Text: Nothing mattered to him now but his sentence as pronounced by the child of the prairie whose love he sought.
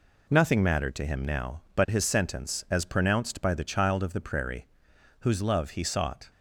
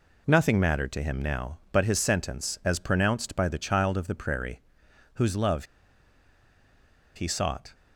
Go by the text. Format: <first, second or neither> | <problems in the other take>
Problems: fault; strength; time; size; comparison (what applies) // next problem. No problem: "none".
first | pauses between "prairie" and "whose"; noticeable; at 4.6 s; 0.54 s long; noticeable in the first // pauses between "love" and "he"; strong; at 5.6 s; 1.5 s long